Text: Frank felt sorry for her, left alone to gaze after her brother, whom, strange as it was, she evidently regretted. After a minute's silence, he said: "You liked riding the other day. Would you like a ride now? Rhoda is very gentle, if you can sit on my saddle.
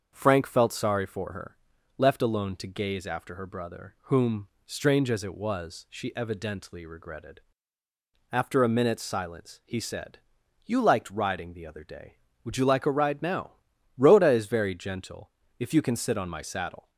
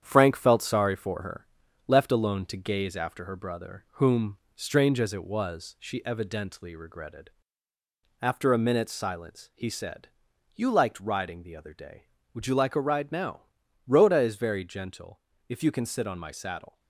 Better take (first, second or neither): first